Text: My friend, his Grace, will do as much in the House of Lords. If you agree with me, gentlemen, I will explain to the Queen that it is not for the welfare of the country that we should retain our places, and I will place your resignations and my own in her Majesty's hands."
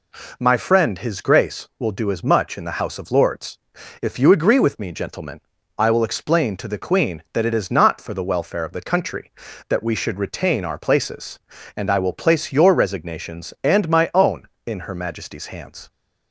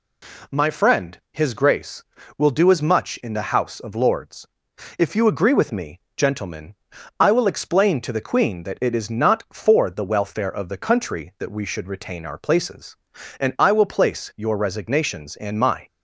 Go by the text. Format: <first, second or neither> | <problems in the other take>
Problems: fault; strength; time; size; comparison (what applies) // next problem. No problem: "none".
first | stops before "own in her Majesty's hands"; at 15.8 s